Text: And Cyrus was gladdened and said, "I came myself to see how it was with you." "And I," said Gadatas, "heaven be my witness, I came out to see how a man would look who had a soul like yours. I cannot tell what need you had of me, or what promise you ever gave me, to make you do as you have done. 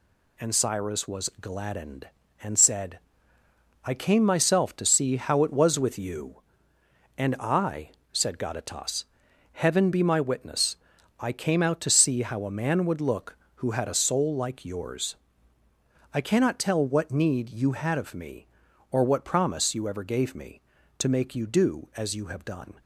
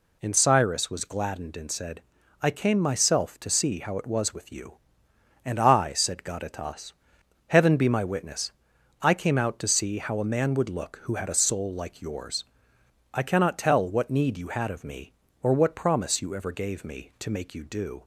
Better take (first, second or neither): first